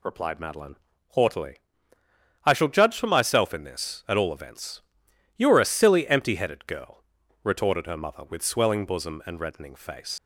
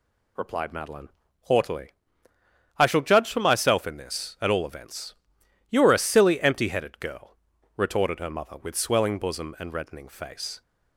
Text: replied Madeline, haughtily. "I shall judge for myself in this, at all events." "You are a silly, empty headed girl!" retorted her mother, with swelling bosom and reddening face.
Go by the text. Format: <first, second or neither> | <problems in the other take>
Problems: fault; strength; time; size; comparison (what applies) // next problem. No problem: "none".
second | leaves "face" unfinished; at 10.1 s; 105 ms